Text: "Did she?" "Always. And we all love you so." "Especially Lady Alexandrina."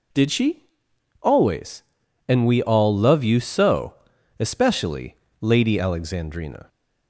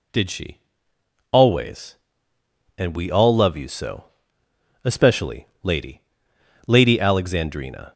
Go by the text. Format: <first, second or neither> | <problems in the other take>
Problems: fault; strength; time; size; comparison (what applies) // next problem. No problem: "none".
first | pauses between "Especially" and "Lady"; slight; at 5.4 s; 0.16 s long; slight in the first // says "Lady" twice; at 6.6 s